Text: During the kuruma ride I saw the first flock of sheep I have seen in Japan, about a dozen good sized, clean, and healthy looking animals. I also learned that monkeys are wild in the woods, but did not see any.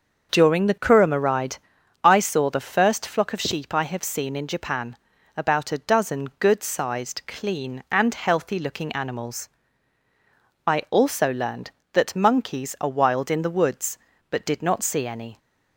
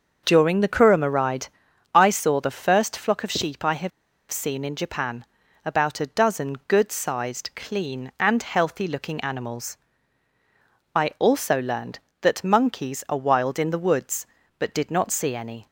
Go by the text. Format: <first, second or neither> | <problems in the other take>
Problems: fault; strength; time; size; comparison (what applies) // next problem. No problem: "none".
first | pauses between "ride" and "I"; at 1.4 s; 0.44 s long; also in the first // pauses between "have" and "seen"; at 3.9 s; 0.39 s long